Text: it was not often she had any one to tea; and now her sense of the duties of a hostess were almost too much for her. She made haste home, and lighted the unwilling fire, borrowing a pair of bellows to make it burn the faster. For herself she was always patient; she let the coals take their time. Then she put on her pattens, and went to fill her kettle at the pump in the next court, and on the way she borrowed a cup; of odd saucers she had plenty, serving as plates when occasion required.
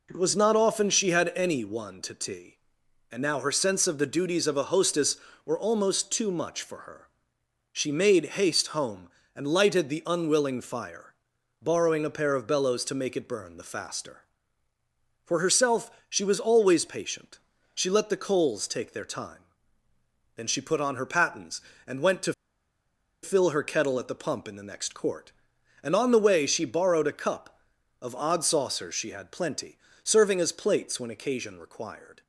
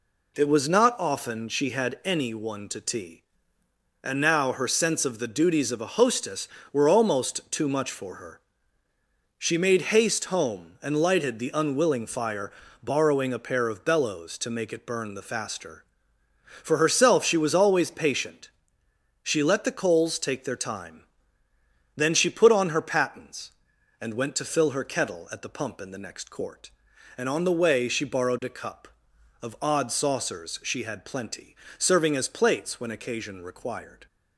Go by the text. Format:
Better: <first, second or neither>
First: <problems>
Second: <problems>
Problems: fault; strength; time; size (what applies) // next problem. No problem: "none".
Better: second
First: pauses between "herself" and "she"; slight; at 15.9 s; 0.18 s long // pauses between "to" and "fill"; noticeable; at 22.3 s; 0.89 s long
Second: none